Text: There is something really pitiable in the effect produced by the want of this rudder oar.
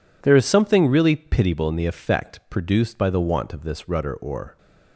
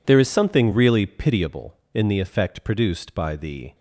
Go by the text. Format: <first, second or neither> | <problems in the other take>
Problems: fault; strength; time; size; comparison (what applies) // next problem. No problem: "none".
first | stops before "want of this rudder oar"; at 3.7 s